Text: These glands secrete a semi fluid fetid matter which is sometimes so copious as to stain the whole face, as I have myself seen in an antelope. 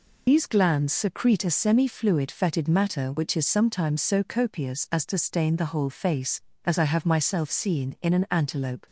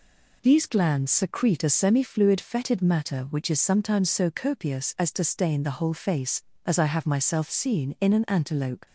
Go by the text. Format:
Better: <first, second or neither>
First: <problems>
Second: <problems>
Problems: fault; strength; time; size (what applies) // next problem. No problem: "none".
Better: second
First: loses the start of "These"; at 0.2 s; 75 ms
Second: none